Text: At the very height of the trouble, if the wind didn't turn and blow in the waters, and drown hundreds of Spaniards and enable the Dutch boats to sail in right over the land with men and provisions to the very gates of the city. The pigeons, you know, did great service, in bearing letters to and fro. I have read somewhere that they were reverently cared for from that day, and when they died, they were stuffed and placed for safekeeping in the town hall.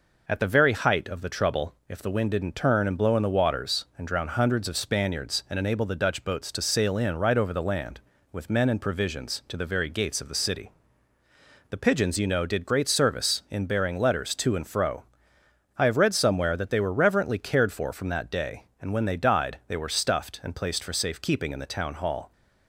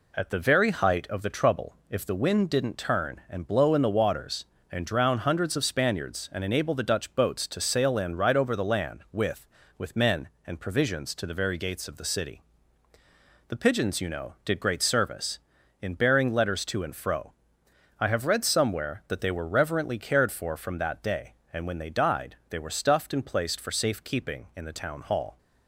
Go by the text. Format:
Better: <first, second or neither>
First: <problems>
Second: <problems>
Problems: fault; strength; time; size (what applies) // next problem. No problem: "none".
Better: first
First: none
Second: says "with" twice; at 9.7 s